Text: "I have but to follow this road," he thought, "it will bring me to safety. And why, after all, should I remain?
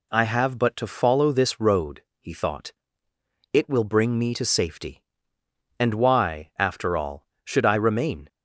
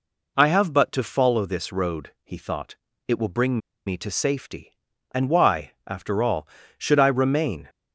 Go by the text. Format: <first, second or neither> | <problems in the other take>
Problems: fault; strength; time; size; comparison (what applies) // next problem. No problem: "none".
first | pauses between "bring" and "me"; slight; at 3.5 s; 0.28 s long